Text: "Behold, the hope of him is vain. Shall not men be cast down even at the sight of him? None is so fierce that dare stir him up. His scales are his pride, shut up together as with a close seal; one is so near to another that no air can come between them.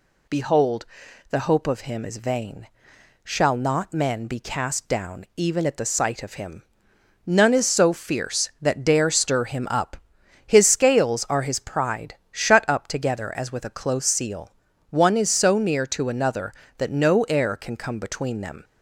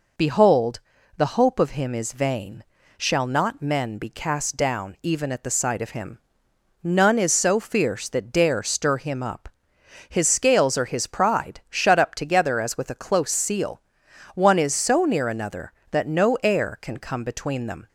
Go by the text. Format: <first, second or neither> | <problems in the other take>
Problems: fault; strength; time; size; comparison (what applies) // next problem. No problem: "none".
first | skips "to"; at 15.2 s